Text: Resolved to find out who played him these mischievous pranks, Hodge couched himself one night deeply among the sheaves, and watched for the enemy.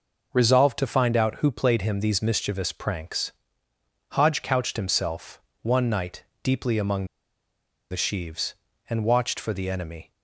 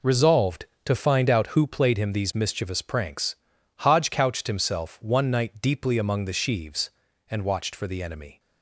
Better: second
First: pauses between "himself" and "one"; slight; at 5.4 s; 0.20 s long // pauses between "night" and "deeply"; slight; at 6.2 s; 0.22 s long // pauses between "among" and "the"; noticeable; at 7.0 s; 0.85 s long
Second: none

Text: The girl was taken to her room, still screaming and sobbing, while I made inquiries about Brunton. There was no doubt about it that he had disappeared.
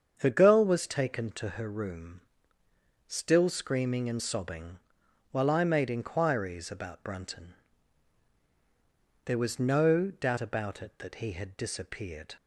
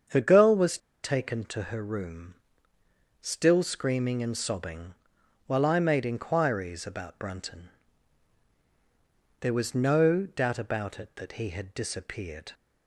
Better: first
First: starts louder than the rest; strong; until 1.1 s; 7.5 dB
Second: starts louder than the rest; strong; until 1.3 s; 7.5 dB // pauses between "was" and "taken"; slight; at 0.7 s; 0.25 s long

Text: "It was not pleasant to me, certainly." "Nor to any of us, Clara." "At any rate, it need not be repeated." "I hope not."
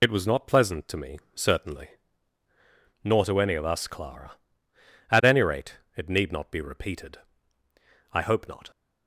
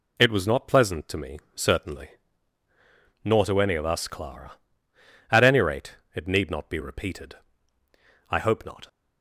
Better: second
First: loses the start of "It"; at 0.0 s; 40 ms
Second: none

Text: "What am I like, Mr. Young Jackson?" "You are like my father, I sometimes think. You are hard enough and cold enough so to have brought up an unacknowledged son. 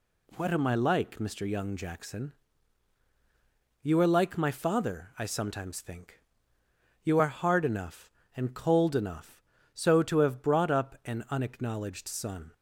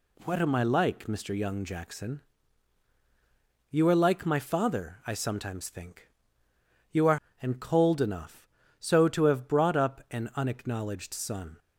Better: first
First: none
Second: skips "hard enough"; at 7.2 s

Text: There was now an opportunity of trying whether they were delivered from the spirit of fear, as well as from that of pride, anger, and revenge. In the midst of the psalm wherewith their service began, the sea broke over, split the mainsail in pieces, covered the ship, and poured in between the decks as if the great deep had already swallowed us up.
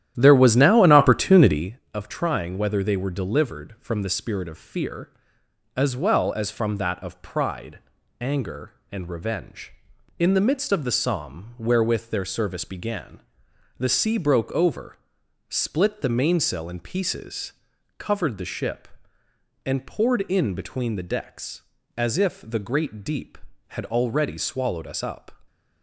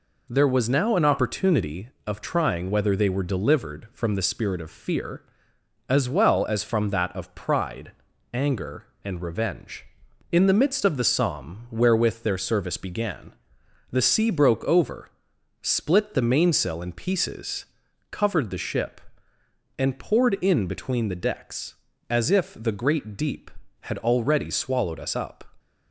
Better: second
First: starts louder than the rest; strong; until 1.7 s; 12 dB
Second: none

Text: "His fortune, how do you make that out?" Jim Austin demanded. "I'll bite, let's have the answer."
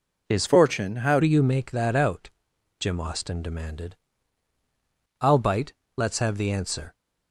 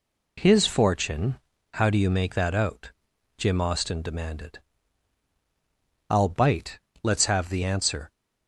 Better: second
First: changes voice from "fortune" to "how"; from 0.4 to 1.2 s; 0.8 s long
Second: none

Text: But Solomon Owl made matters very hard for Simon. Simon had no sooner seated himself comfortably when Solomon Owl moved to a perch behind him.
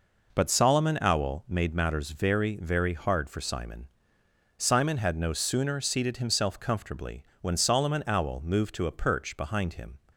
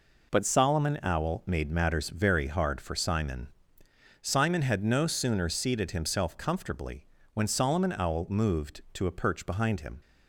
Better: second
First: says "very" twice; at 2.5 s // pauses between "comfortably" and "when"; slight; at 7.2 s; 0.18 s long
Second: pauses between "comfortably" and "when"; slight; at 7.0 s; 0.26 s long

